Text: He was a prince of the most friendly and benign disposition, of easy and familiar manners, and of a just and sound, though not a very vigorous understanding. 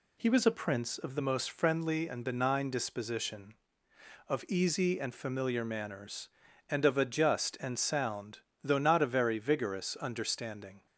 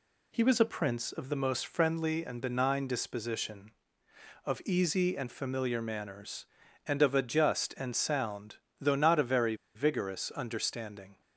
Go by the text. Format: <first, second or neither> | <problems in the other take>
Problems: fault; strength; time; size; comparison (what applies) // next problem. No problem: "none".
first | pauses between "very" and "vigorous"; slight; at 9.5 s; 0.20 s long